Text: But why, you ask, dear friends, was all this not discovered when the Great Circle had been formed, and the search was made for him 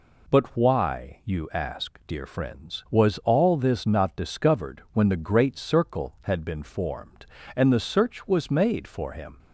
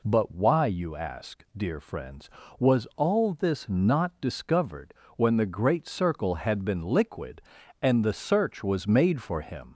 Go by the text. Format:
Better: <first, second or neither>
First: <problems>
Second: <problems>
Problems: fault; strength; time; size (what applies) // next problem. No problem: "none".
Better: first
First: none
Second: pauses between "discovered" and "when"; slight; at 4.9 s; 0.22 s long // says "liquid" for "formed"; at 6.8 s